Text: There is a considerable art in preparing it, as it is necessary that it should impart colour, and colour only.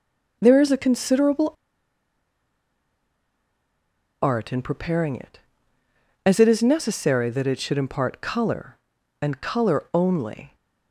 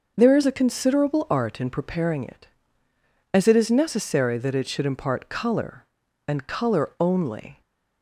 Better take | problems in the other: second | pauses between "considerable" and "art"; strong; at 1.5 s; 2.7 s long

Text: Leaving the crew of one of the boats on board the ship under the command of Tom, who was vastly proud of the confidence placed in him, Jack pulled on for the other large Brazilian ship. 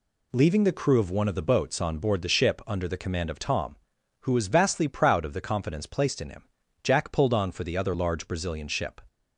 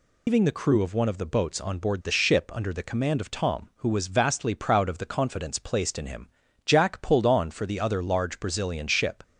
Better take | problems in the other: first | loses the start of "Leaving"; at 0.2 s; 155 ms

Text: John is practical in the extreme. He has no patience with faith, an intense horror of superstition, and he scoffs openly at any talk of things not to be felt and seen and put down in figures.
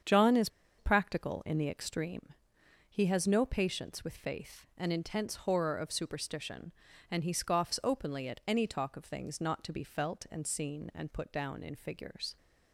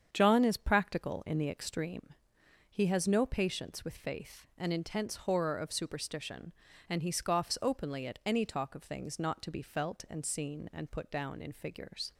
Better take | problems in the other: second | starts louder than the rest; strong; until 1.3 s; 7.5 dB; strong in the second // pauses between "is" and "practical"; slight; at 0.4 s; 0.29 s long

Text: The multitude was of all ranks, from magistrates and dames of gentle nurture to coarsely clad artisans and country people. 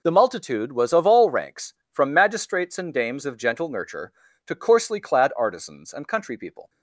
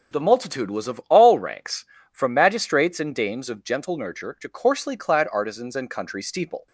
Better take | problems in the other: first | starts louder than the rest; until 1.2 s; 7 dB // says "steeple" for "people"; at 6.2 s

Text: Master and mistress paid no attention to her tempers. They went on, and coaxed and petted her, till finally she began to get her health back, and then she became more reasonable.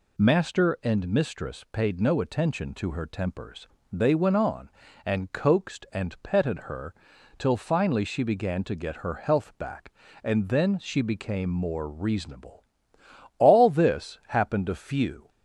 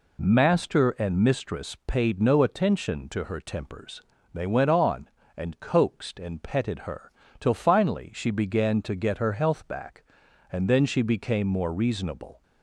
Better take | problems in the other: second | goes on to say "All this happened a few"; strong; from 13.3 s on; 1.9 s long

